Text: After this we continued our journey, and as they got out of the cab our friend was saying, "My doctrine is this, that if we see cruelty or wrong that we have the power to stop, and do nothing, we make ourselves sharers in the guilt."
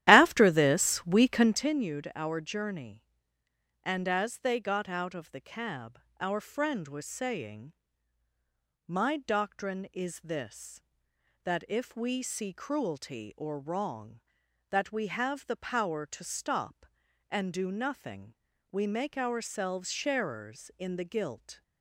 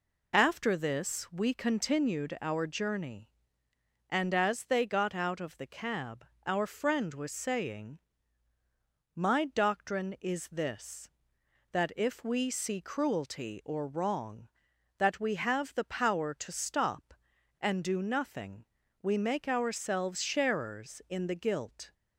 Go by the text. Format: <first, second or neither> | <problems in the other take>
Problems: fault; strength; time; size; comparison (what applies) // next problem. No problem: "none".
second | starts louder than the rest; strong; until 1.7 s; 13 dB // pauses between "cab" and "our"; slight; at 6.0 s; 0.18 s long; slight in the second